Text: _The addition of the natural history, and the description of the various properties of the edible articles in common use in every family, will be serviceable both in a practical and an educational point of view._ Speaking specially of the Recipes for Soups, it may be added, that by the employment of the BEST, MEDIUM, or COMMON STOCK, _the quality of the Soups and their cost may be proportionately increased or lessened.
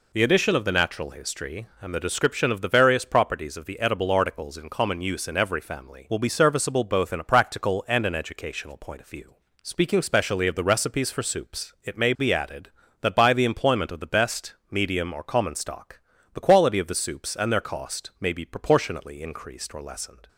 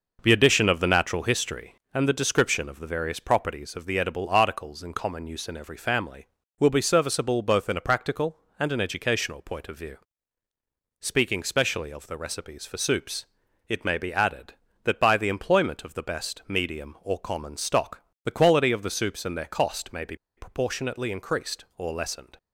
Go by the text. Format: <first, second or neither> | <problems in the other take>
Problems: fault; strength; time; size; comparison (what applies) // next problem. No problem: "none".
first | pauses between "be" and "proportionately"; slight; at 20.1 s; 0.20 s long